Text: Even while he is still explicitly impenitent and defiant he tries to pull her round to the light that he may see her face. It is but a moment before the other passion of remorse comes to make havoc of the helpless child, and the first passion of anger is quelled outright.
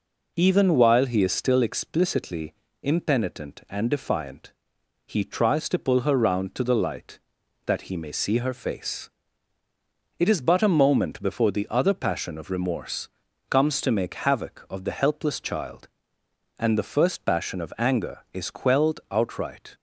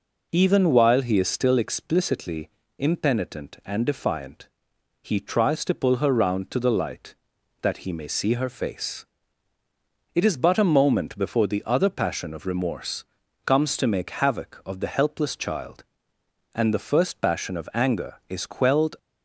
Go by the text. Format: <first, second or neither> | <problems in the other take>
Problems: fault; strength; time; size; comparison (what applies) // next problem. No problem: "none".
first | pauses between "explicitly" and "impenitent"; slight; at 2.4 s; 0.28 s long; slight in the first // pauses between "defiant" and "he"; noticeable; at 4.4 s; 0.54 s long; noticeable in the first // pauses between "remorse" and "comes"; at 13.0 s; 0.40 s long; also in the first // stops before "outright"; at 18.9 s